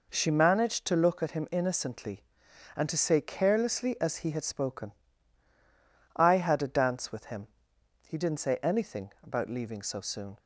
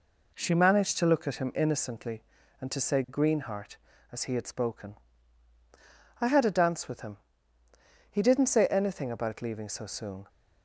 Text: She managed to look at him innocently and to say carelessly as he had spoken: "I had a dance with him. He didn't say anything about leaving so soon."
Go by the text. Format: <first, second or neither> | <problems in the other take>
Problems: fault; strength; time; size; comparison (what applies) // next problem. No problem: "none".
first | says "greenheart" for "carelessly"; at 3.0 s